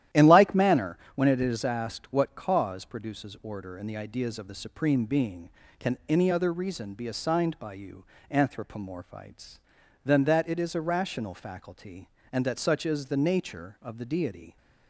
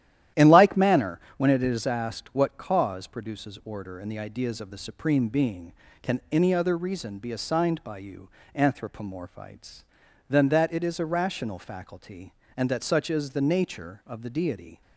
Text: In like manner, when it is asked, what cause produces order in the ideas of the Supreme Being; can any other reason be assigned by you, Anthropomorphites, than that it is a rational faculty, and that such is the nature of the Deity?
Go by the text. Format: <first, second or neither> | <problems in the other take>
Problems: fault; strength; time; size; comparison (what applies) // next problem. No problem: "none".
neither | starts louder than the rest; strong; the same in both